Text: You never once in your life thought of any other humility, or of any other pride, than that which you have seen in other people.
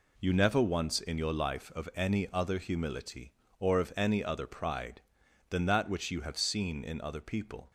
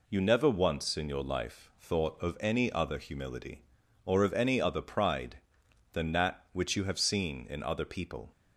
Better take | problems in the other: second | skips "thought"; at 1.7 s

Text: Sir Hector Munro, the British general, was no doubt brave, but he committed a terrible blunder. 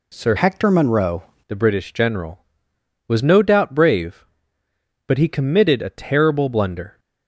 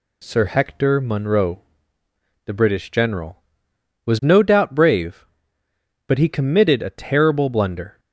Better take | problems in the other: second | changes voice from "Hector" to "Munro"; from 0.3 to 1.2 s; 0.9 s long

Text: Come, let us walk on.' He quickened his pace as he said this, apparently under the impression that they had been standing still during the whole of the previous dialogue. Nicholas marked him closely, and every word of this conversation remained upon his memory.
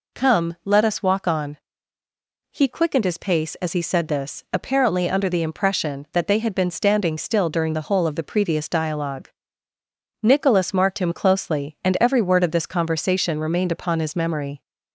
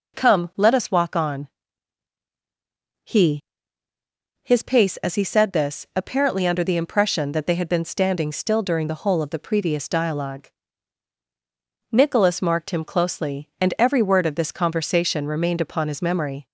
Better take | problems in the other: first | skips "quickened"; at 3.9 s

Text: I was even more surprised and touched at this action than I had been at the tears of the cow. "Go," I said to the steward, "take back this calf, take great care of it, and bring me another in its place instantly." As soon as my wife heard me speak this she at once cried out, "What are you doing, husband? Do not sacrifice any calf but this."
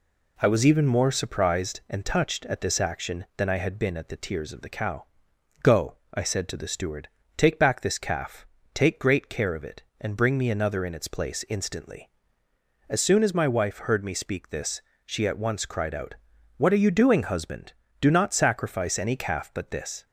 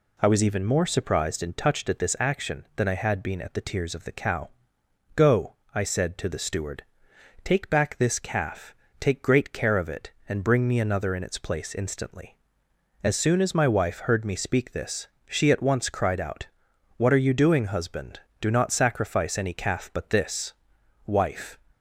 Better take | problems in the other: first | pauses between "this" and "she"; slight; at 15.0 s; 0.22 s long; slight in the first // goes on to say "Wife"; from 21.0 s on; 0.52 s long

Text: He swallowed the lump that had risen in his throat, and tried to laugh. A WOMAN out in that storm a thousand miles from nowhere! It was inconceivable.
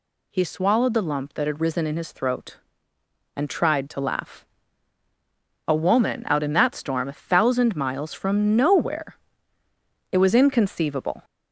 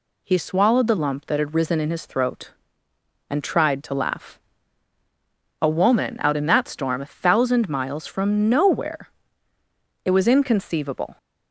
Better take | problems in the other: second | gets louder; slight; throughout; 3 dB

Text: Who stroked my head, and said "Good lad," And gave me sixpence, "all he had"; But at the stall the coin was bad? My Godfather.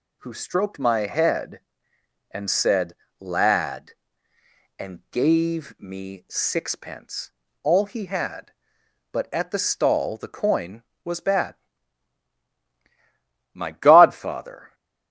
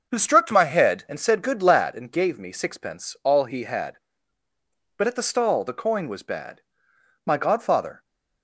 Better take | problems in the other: second | skips "Good"; at 3.0 s

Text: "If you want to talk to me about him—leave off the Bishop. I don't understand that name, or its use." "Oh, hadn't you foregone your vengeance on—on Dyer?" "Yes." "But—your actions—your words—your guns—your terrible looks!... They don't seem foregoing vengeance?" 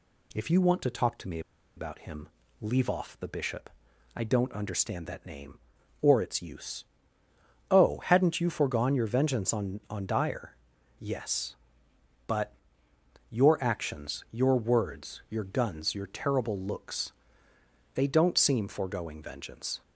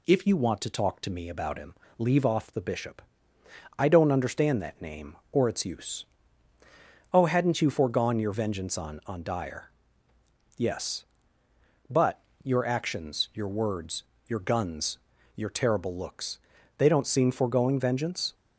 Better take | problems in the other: second | pauses between "me" and "about"; at 1.3 s; 0.36 s long

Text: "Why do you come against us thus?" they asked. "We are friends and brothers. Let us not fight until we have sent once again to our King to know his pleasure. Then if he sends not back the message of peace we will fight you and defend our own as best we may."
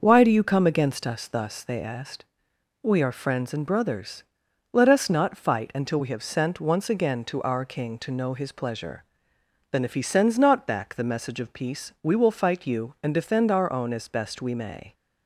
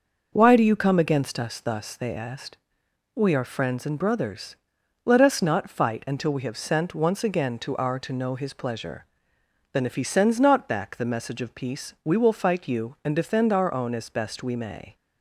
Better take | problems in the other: first | starts louder than the rest; noticeable; until 1.3 s; 6 dB; noticeable in the first // skips "King"; at 8.0 s

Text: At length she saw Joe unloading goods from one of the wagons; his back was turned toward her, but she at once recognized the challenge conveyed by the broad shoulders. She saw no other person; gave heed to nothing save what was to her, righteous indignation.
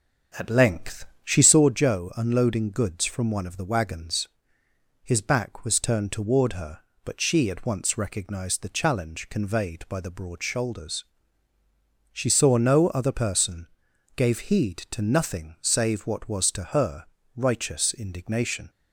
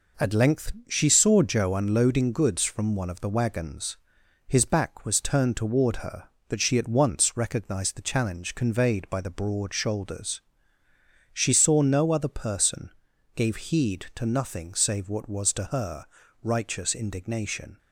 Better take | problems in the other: second | starts louder than the rest; until 1.7 s; 7 dB // pauses between "length" and "she"; slight; at 1.0 s; 0.18 s long; slight in the second

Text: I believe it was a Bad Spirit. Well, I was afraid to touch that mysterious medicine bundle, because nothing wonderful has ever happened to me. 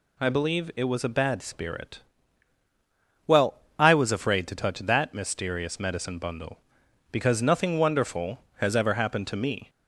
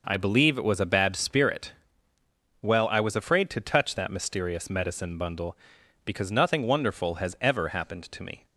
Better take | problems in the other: neither | none

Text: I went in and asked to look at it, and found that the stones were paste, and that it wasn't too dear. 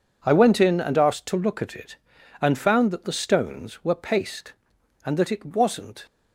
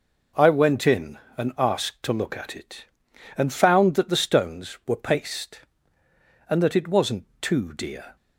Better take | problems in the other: second | stops before "too dear"; at 6.0 s

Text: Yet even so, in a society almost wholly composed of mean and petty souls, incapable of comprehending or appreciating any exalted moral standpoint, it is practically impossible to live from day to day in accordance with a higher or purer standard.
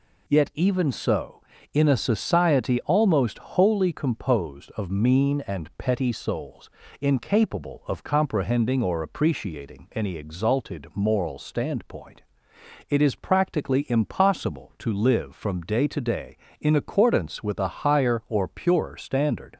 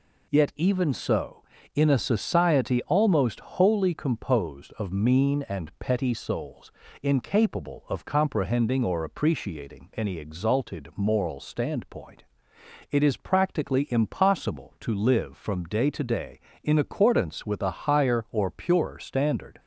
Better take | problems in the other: neither | none

